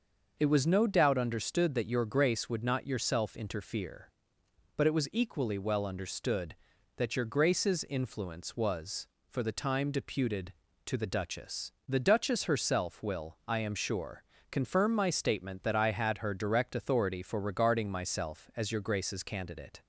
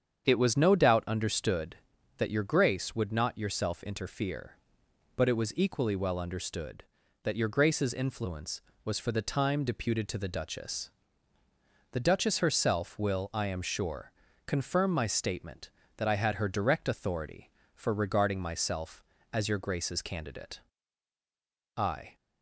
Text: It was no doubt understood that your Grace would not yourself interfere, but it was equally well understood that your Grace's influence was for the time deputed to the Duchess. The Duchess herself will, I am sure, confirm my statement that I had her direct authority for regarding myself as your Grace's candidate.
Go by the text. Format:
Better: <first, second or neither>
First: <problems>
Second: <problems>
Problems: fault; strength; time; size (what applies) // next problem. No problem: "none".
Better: first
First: none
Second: starts louder than the rest; strong; until 1.2 s; 8 dB // goes on to say "I"; slight; from 21.7 s on; 0.38 s long